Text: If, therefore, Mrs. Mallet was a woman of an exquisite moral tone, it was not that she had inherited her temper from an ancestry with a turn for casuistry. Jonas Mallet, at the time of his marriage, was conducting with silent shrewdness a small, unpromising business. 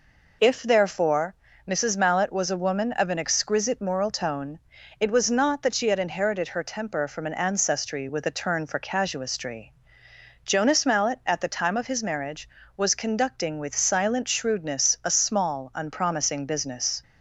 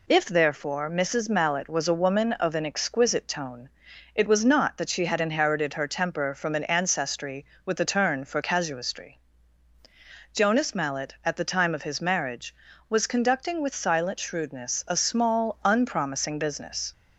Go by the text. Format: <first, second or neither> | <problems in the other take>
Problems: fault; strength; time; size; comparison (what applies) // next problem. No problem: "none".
first | skips "moral"; at 3.2 s